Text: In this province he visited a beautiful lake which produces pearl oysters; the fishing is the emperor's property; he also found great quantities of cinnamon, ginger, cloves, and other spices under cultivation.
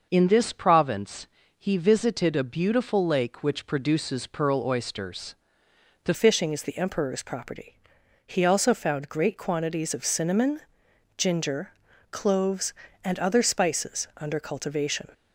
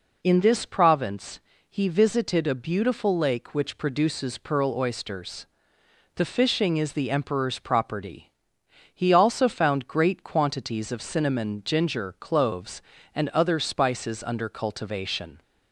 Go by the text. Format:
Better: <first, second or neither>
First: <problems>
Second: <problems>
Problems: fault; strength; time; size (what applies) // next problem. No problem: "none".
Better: second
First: pauses between "province" and "he"; slight; at 1.2 s; 0.32 s long // changes voice at "fishing"; from 6.1 s on; 9.0 s long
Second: pauses between "province" and "he"; slight; at 1.3 s; 0.30 s long